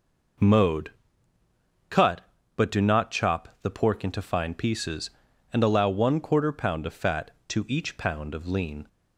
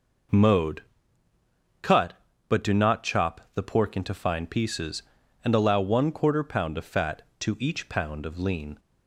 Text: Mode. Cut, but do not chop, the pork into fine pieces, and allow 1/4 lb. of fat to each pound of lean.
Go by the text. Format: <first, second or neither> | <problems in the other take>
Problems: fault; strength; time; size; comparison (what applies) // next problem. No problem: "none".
neither | none